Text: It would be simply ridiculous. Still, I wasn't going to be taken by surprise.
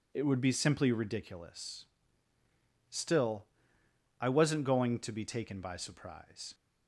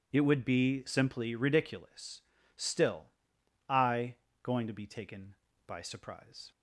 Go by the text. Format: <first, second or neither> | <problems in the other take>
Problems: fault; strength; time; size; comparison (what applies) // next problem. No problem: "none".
first | skips "wasn't"; at 4.2 s